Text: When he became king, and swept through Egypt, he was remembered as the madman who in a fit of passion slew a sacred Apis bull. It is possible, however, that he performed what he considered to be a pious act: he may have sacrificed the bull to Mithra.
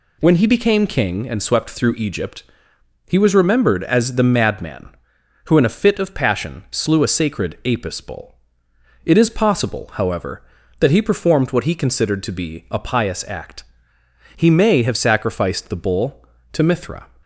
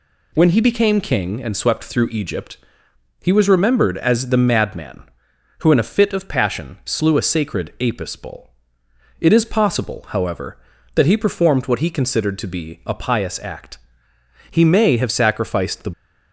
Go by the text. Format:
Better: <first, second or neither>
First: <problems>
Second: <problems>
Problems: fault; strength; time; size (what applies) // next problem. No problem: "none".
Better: first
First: none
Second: stops before "bull to Mithra"; at 15.9 s